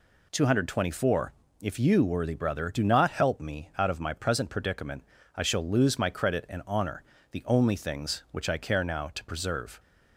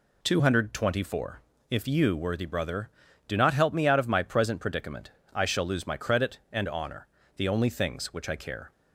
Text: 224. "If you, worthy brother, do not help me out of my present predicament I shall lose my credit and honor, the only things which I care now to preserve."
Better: first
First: pauses between "predicament" and "I"; slight; at 5.0 s; 0.30 s long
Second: pauses between "predicament" and "I"; slight; at 5.0 s; 0.24 s long // stops before "now to preserve"; at 8.7 s

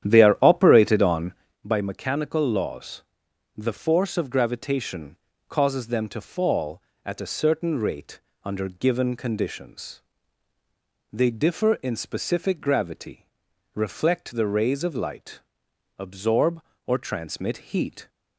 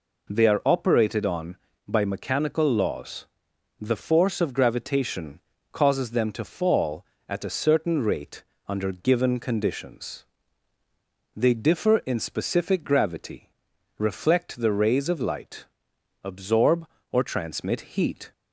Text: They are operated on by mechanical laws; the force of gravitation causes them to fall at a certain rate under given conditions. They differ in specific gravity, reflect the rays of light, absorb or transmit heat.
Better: second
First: starts louder than the rest; strong; until 1.6 s; 10.5 dB // pauses between "gravitation" and "causes"; slight; at 5.1 s; 0.32 s long // pauses between "rate" and "under"; slight; at 8.1 s; 0.24 s long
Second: pauses between "gravitation" and "causes"; slight; at 5.3 s; 0.32 s long // pauses between "rate" and "under"; slight; at 8.4 s; 0.24 s long

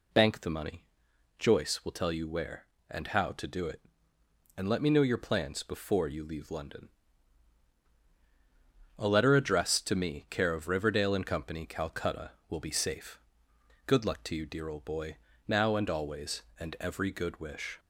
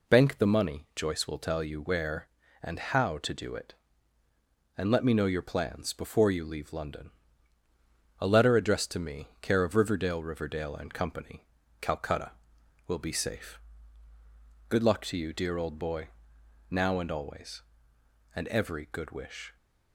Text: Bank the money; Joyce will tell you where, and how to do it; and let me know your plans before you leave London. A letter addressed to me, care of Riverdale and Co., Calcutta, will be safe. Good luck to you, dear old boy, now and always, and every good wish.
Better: first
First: none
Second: says "Riverdale" twice; at 10.2 s

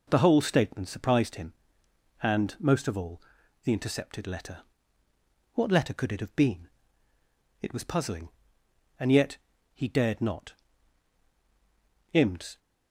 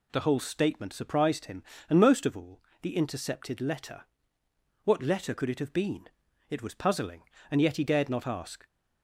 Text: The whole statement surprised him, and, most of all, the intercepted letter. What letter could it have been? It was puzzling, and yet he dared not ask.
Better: second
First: pauses between "yet" and "he"; at 9.3 s; 0.38 s long // says "imds" for "ask"; at 12.1 s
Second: none

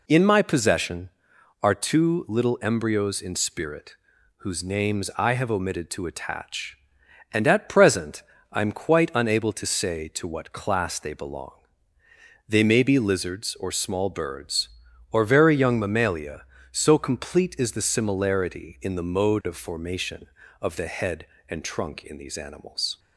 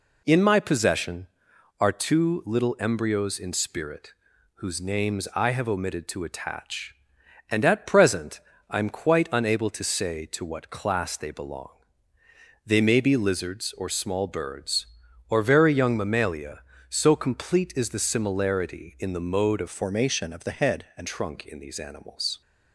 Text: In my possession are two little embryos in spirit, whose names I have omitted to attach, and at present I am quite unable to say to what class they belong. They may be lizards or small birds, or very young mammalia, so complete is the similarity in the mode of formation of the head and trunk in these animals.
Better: first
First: pauses between "present" and "I"; slight; at 8.2 s; 0.30 s long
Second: pauses between "present" and "I"; slight; at 8.3 s; 0.30 s long // changes voice from "formation" to "and"; from 19.6 to 21.0 s; 1.4 s long

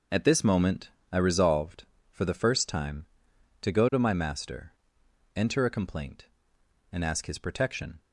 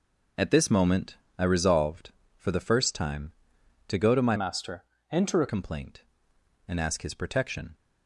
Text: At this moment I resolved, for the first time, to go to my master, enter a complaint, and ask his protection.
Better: first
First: pauses between "moment" and "I"; slight; at 0.8 s; 0.22 s long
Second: pauses between "moment" and "I"; slight; at 1.1 s; 0.22 s long // changes voice from "master" to "a"; from 4.3 to 5.4 s; 1.1 s long

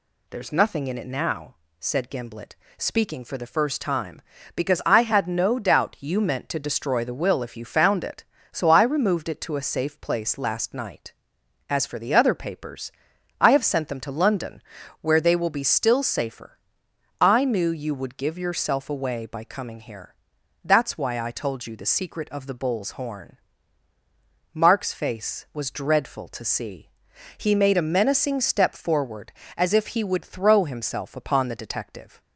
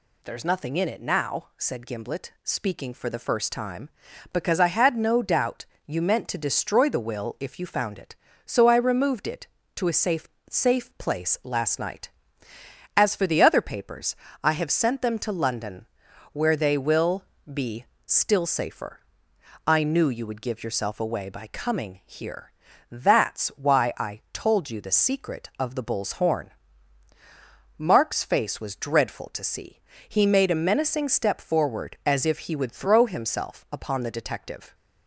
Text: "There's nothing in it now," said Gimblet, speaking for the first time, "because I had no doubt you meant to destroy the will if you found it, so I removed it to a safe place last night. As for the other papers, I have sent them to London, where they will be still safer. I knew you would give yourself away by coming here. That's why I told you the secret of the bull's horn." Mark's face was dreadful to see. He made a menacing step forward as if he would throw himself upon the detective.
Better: first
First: none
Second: pauses between "doubt" and "you"; slight; at 5.6 s; 0.22 s long // says "safe" twice; at 10.4 s // pauses between "will" and "be"; slight; at 17.2 s; 0.28 s long // pauses between "be" and "still"; slight; at 17.8 s; 0.18 s long

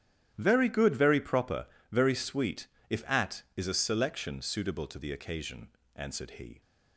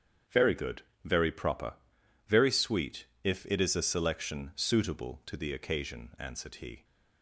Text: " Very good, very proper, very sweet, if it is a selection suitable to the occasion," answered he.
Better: second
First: starts louder than the rest; strong; until 1.3 s; 10.5 dB // says "at" for "it"; at 3.0 s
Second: starts louder than the rest; strong; until 1.5 s; 8.5 dB

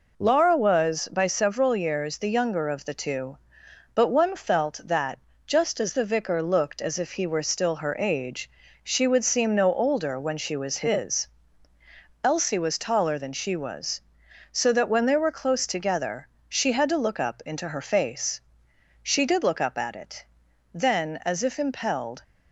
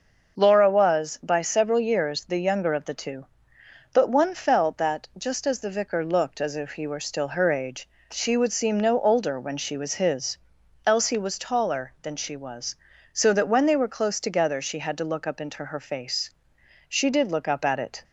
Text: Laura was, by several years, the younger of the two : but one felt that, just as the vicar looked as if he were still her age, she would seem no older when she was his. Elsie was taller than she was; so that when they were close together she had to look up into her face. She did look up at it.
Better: second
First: pauses between "together" and "she"; slight; at 16.2 s; 0.22 s long // goes on to say "Then as if impelled"; from 20.7 s on; 1.5 s long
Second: none

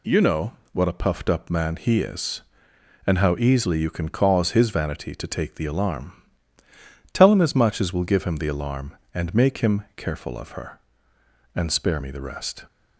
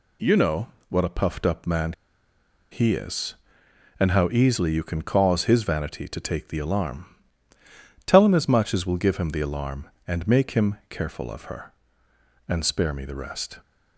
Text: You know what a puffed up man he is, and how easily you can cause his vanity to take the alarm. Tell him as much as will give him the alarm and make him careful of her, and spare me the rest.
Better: first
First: pauses between "know" and "what"; slight; at 0.5 s; 0.22 s long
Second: pauses between "know" and "what"; slight; at 0.6 s; 0.24 s long // pauses between "man" and "he"; noticeable; at 1.9 s; 0.78 s long

